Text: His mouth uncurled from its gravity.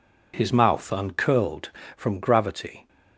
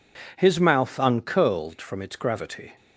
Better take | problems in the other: second | skips "its"; at 2.1 s

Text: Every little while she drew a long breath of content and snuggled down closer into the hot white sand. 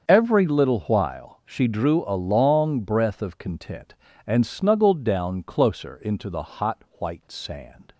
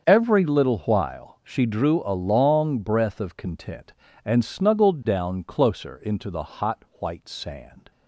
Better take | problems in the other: neither | starts louder than the rest; the same in both // pauses between "hot" and "white"; slight; the same in both

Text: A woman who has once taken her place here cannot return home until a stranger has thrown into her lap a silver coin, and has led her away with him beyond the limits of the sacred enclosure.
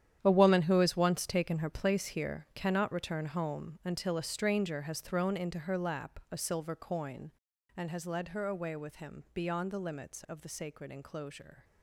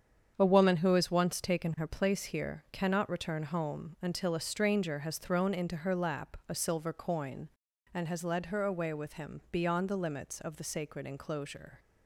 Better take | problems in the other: second | gets quieter; strong; throughout; 13 dB // starts louder than the rest; strong; until 1.2 s; 10 dB; strong in the second

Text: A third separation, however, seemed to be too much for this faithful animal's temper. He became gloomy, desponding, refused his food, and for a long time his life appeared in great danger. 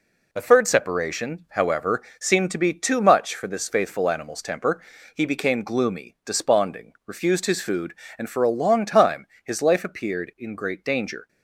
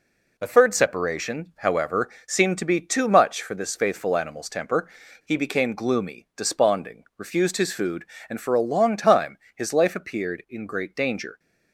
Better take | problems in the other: neither | pauses between "time" and "his"; slight; the same in both

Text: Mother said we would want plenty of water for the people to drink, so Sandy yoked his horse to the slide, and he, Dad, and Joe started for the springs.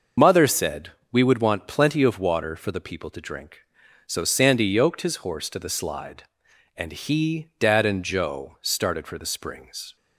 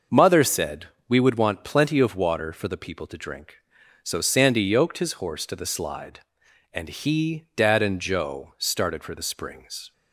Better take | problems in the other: second | loses the start of "Mother"; at 0.1 s; 30 ms // pauses between "said" and "we"; slight; at 0.8 s; 0.22 s long; slight in the second

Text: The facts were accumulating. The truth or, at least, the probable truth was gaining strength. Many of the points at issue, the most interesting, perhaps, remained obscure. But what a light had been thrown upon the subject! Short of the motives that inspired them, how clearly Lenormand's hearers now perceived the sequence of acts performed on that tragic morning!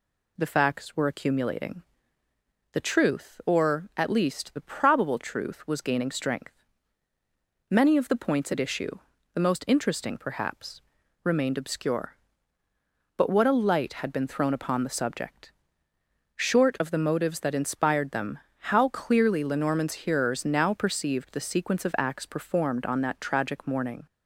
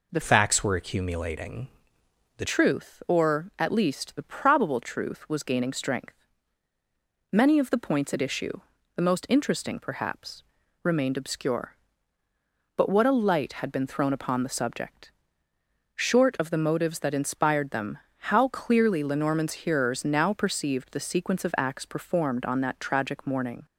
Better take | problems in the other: first | changes voice from "facts" to "The"; from 0.2 to 2.4 s; 2.2 s long

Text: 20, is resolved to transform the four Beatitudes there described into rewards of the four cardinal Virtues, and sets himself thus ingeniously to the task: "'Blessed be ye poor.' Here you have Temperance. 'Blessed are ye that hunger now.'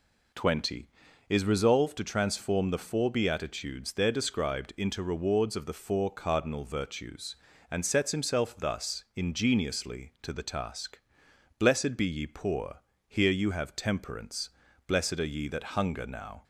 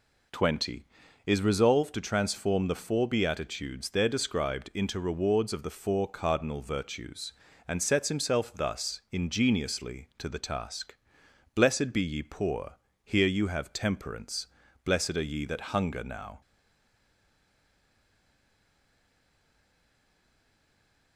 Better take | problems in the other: first | stays silent after the last word; strong; from 16.4 s on; 4.7 s long

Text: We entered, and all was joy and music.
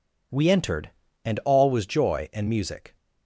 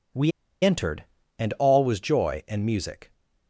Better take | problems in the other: first | pauses between "We" and "entered"; slight; at 0.3 s; 0.33 s long

